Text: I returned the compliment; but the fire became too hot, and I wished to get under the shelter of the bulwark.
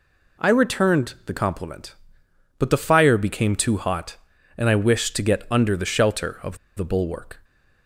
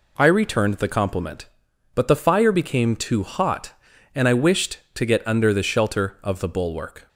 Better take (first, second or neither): second